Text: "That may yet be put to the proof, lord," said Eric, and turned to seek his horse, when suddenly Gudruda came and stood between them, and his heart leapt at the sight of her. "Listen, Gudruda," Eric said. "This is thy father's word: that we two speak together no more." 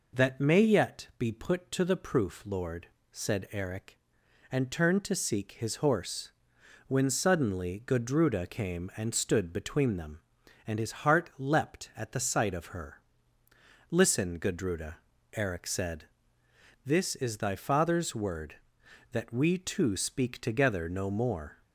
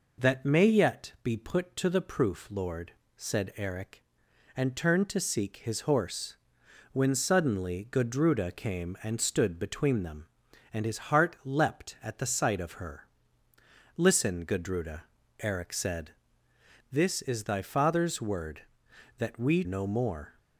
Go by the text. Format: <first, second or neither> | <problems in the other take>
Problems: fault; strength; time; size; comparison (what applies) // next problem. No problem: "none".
first | skips "two speak together"; at 19.6 s